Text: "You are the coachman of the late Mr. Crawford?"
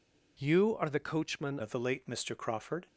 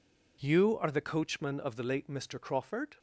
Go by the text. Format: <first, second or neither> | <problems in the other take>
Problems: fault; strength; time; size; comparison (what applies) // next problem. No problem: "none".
second | changes voice at "of"; from 1.6 s on; 1.2 s long